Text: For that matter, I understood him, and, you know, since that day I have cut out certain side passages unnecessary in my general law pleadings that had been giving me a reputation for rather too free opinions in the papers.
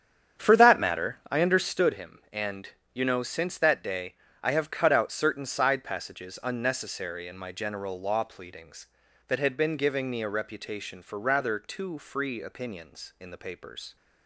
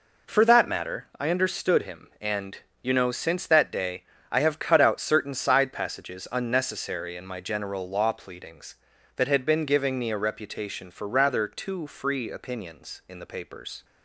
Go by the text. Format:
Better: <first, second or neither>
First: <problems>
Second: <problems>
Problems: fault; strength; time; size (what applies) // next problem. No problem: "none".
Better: second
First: starts louder than the rest; strong; until 1.9 s; 8.5 dB // pauses between "day" and "I"; slight; at 4.1 s; 0.30 s long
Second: pauses between "day" and "I"; slight; at 4.0 s; 0.30 s long